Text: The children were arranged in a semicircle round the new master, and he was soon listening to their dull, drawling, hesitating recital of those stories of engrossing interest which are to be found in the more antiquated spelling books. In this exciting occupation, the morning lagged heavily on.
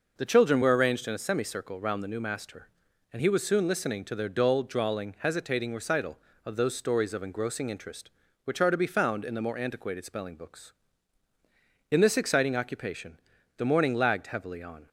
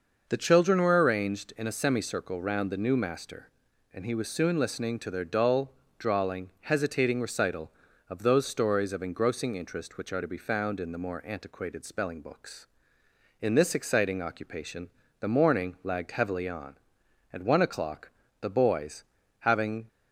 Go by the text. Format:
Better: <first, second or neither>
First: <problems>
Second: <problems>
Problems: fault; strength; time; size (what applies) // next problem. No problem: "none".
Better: first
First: none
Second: goes on to say "At one o'clock the boys having"; strong; from 17.3 s on; 2.5 s long